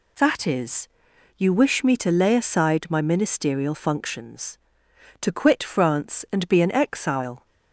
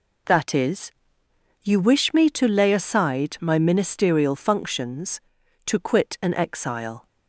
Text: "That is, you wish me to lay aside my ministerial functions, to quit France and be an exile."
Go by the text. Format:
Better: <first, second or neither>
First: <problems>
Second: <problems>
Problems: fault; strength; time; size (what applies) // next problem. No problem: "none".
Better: first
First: none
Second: skips "France and be"; at 6.1 s